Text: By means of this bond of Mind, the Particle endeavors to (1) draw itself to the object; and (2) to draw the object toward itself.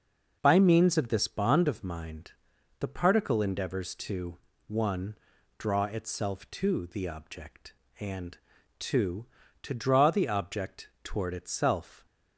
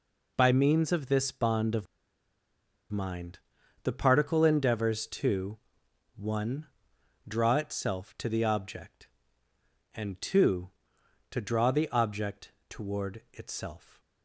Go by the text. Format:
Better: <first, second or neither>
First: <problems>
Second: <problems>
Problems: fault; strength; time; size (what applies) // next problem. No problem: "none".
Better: first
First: pauses between "object" and "toward"; slight; at 10.8 s; 0.16 s long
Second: pauses between "of" and "Mind"; at 1.8 s; 1.0 s long // pauses between "object" and "toward"; slight; at 12.5 s; 0.18 s long